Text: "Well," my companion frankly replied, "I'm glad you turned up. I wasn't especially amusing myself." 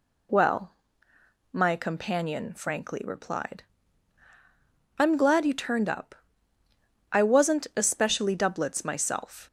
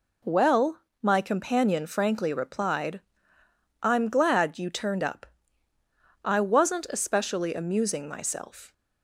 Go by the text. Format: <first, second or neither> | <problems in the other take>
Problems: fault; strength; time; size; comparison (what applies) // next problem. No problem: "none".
second | says "doublets" for "amusing"; at 8.3 s